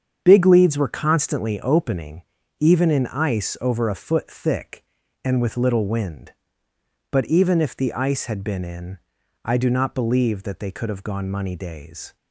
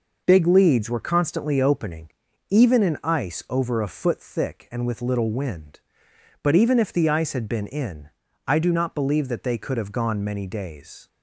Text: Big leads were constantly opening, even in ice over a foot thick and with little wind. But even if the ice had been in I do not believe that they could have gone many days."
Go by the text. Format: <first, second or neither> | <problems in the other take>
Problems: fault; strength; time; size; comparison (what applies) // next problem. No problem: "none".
second | starts louder than the rest; strong; until 1.2 s; 8 dB // pauses between "in" and "I"; noticeable; at 8.9 s; 0.50 s long; slight in the second // says "money" for "many"; at 11.3 s